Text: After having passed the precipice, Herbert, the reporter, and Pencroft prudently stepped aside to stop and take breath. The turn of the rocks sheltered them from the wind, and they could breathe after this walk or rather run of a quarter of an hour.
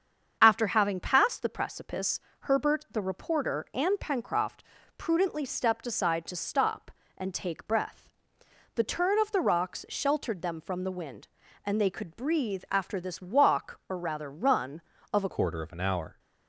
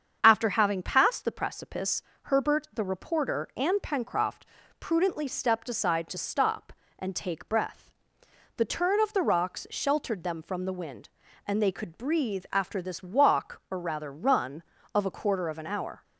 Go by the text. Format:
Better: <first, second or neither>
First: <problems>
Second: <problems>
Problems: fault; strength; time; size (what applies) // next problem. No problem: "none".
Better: second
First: starts louder than the rest; strong; until 1.4 s; 7.5 dB // pauses between "Pencroft" and "prudently"; slight; at 4.6 s; 0.34 s long // changes voice at "quarter"; from 15.2 s on; 0.9 s long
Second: starts louder than the rest; strong; until 1.2 s; 7.5 dB // pauses between "Pencroft" and "prudently"; slight; at 4.4 s; 0.34 s long